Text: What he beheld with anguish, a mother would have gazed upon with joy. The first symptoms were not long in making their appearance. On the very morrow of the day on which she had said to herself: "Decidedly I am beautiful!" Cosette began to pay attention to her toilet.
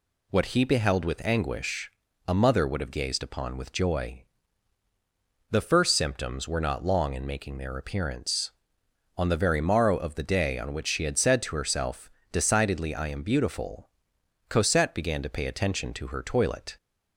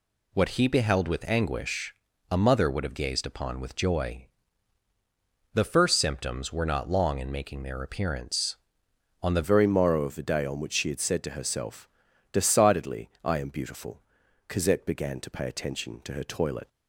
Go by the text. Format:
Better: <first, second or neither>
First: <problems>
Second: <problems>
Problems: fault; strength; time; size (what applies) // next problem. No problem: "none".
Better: first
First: none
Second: changes voice at "very"; from 9.4 s on; 7.2 s long